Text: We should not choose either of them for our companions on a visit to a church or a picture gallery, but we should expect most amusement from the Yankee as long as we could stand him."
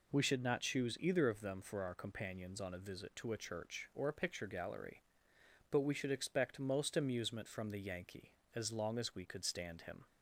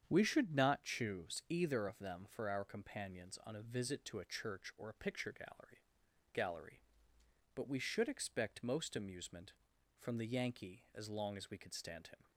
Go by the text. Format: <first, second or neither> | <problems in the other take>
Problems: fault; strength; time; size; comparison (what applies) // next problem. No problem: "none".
first | starts louder than the rest; strong; until 1.1 s; 8 dB // says "gallery" twice; at 6.3 s